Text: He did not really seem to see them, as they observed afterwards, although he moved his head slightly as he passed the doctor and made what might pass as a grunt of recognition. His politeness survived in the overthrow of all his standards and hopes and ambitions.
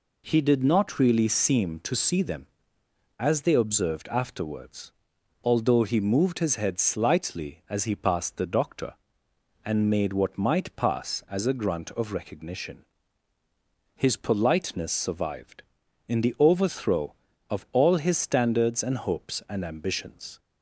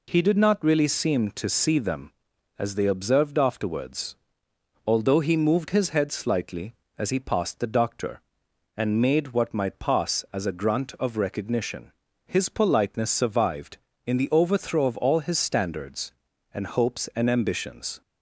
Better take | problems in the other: neither | none

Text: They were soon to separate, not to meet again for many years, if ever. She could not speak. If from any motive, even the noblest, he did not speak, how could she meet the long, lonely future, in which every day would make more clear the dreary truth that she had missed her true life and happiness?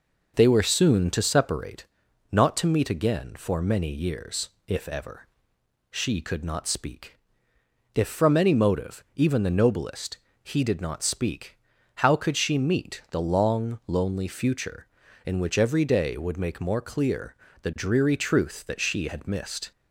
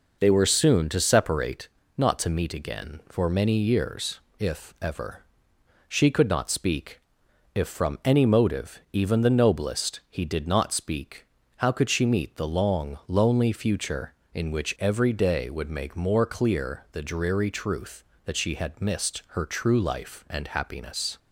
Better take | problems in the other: second | pauses between "clear" and "the"; slight; at 17.3 s; 0.26 s long // stops before "her true life and happiness"; at 19.7 s

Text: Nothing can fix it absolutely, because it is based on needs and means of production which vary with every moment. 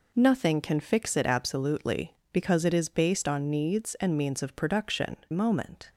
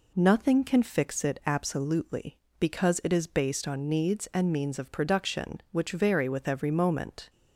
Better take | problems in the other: second | skips "which vary with every"; at 5.2 s

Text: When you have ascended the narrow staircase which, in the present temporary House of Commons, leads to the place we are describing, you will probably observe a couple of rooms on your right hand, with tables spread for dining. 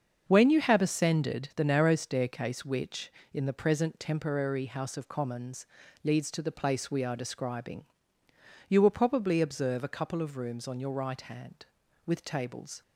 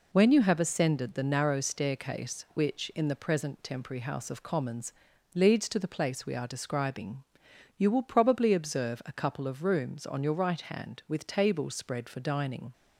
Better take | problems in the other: second | starts louder than the rest; until 1.2 s; 6.5 dB // stops before "spread for dining"; at 12.8 s

